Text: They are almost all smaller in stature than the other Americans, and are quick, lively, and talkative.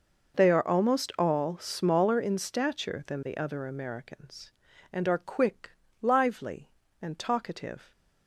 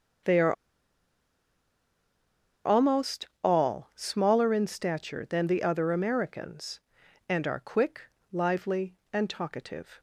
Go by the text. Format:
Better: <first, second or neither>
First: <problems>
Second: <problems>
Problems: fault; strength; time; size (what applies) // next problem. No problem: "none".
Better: first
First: none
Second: starts louder than the rest; until 3.5 s; 7 dB // pauses between "are" and "almost"; strong; at 0.5 s; 2.1 s long // pauses between "almost" and "all"; slight; at 3.2 s; 0.18 s long